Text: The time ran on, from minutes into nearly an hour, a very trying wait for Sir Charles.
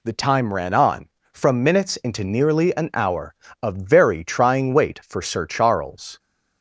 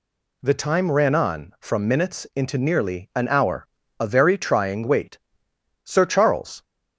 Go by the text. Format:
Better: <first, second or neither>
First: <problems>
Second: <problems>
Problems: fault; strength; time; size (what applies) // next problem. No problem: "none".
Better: first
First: none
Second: skips "for"; at 5.5 s